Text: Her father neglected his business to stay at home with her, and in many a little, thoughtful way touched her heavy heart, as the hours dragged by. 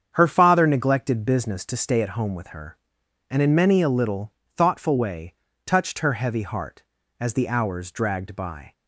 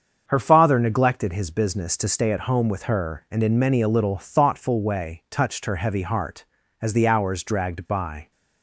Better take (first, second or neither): second